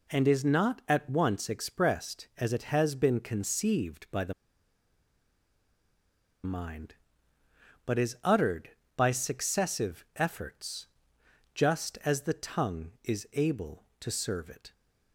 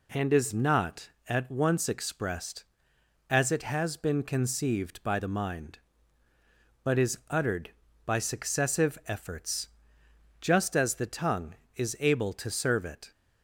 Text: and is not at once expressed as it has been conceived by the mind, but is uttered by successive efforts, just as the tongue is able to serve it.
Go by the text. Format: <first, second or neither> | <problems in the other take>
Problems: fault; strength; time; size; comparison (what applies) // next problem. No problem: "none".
second | pauses between "the" and "mind"; strong; at 4.3 s; 2.1 s long